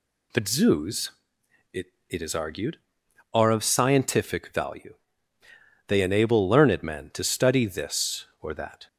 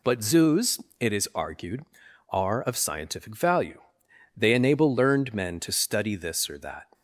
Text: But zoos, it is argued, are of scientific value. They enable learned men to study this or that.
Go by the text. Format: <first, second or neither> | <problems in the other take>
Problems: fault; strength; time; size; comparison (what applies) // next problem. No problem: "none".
second | says "it" twice; at 2.0 s